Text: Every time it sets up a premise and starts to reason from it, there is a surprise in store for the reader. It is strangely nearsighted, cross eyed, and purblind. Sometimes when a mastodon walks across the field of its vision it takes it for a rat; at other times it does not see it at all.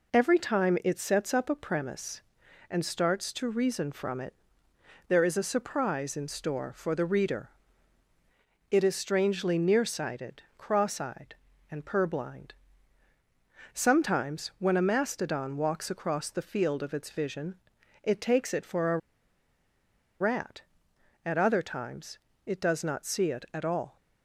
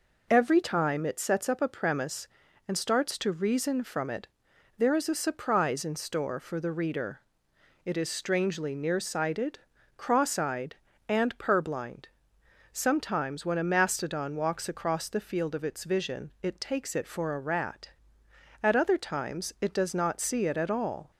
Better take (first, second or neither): second